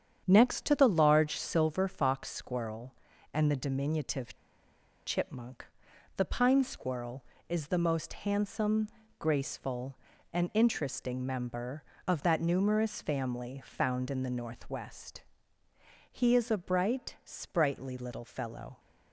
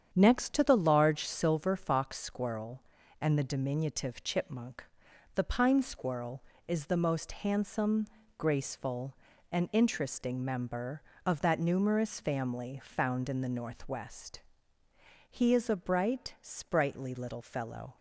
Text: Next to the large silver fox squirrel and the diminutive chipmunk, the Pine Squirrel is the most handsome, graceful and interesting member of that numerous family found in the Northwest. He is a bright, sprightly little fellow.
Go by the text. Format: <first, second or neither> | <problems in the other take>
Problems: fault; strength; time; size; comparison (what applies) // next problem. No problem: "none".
second | starts louder than the rest; strong; until 1.2 s; 8 dB; strong in the second // pauses between "diminutive" and "chipmunk"; noticeable; at 4.3 s; 0.69 s long